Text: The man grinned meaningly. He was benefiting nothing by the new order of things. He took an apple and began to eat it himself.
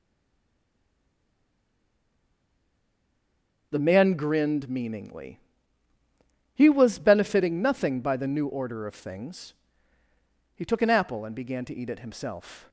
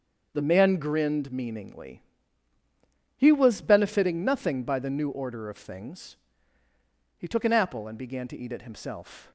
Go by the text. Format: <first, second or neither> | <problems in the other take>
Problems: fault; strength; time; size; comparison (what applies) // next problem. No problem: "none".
second | stays silent before the first word; strong; until 3.7 s; 3.7 s long // starts louder than the rest; until 4.7 s; 6.5 dB; also in the second